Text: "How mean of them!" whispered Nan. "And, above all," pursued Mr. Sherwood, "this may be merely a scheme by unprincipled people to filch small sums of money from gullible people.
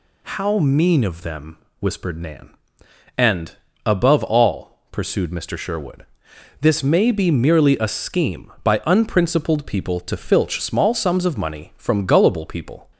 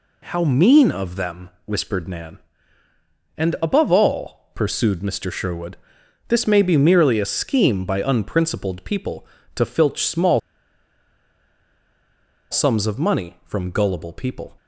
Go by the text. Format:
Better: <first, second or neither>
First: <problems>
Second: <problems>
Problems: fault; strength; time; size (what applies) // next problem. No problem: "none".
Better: first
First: none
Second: pauses between "small" and "sums"; strong; at 10.3 s; 2.1 s long